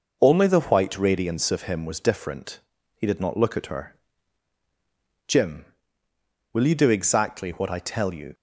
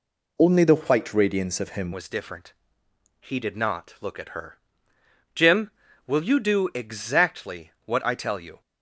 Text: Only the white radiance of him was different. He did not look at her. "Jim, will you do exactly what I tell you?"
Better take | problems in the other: first | changes voice at "was"; from 1.9 s on; 6.7 s long

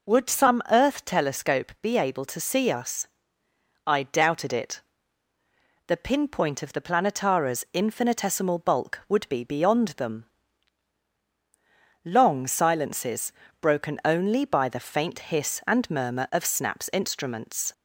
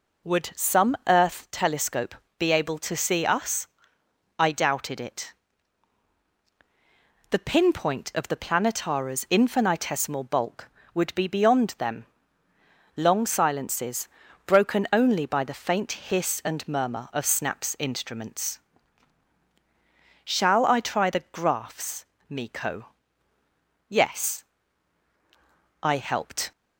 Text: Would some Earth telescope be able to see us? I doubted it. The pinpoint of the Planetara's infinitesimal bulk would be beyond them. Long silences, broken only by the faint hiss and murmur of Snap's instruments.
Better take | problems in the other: first | pauses between "telescope" and "be"; slight; at 2.1 s; 0.24 s long // goes on to say "Shall I try the graphs Miko Yes I helped"; strong; from 20.2 s on; 6.2 s long

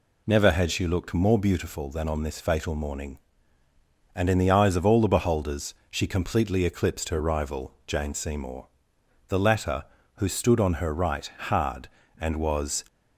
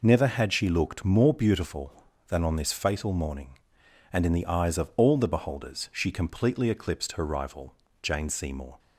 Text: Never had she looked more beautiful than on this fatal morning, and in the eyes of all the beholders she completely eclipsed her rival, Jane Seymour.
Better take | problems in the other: second | pauses between "beholders" and "she"; slight; at 5.7 s; 0.16 s long // goes on to say "The latter who stood on her right hard and was"; strong; from 9.2 s on; 3.5 s long

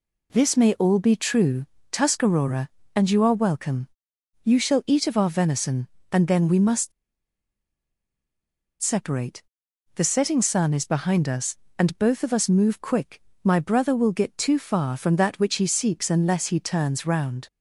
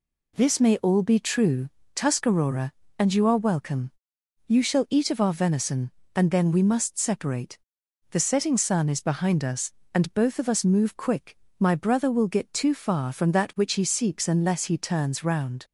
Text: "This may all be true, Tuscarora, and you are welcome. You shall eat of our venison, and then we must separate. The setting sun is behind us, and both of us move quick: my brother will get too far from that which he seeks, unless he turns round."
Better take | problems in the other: second | pauses between "must" and "separate"; strong; at 6.9 s; 1.9 s long

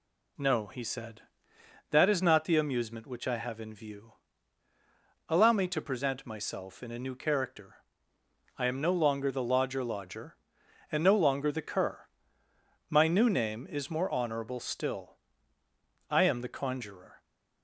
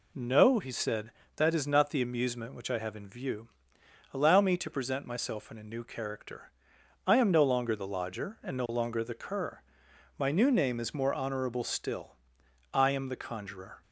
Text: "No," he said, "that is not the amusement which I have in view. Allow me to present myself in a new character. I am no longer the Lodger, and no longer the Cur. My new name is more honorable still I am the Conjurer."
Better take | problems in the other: second | says "Lodger" twice; at 9.8 s // pauses between "still" and "I"; noticeable; at 15.1 s; 0.90 s long; noticeable in the second

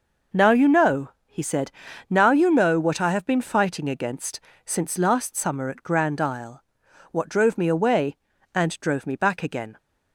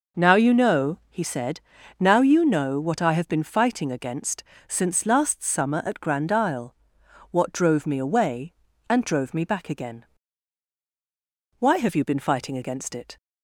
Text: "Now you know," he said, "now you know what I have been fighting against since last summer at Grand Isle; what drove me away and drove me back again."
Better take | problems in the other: first | pauses between "against" and "since"; slight; at 4.4 s; 0.26 s long; slight in the first // goes on to say "Why have you been fighting against it"; from 11.5 s on; 1.5 s long

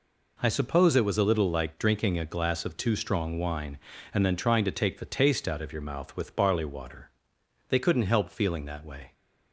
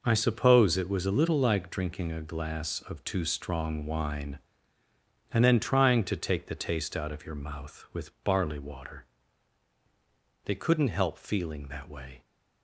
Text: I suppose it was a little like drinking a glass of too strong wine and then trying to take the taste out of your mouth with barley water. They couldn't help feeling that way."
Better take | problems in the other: neither | none

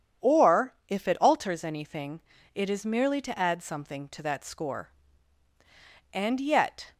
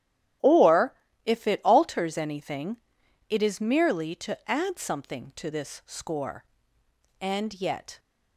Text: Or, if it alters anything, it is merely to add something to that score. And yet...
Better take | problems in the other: first | starts louder than the rest; strong; until 1.7 s; 12 dB // says "this" for "that"; at 5.5 s

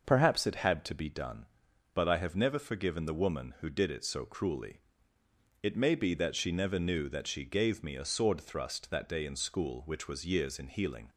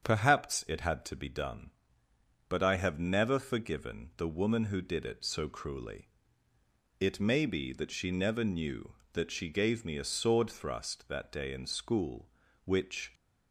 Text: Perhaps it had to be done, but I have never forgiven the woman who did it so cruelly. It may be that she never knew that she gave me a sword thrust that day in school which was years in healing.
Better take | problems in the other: first | starts louder than the rest; strong; until 1.0 s; 7.5 dB; noticeable in the first // stops before "was years in healing"; at 13.1 s

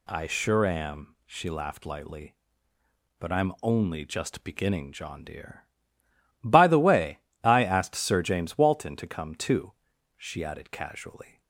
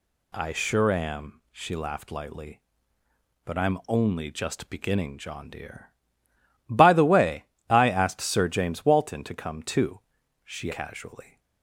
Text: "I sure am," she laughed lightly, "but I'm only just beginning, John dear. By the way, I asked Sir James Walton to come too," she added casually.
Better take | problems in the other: first | skips "added"; at 10.7 s

